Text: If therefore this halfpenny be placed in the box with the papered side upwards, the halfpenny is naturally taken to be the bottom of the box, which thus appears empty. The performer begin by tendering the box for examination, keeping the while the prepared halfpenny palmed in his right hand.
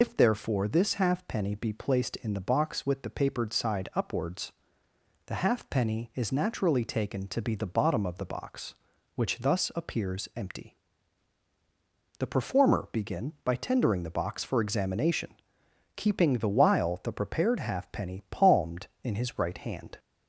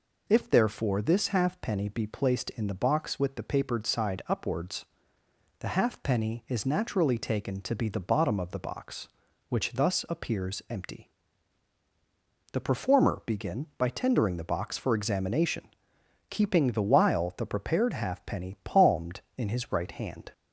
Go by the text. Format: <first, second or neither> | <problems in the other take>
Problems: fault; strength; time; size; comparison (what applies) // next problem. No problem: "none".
second | loses the start of "If"; at 0.0 s; 55 ms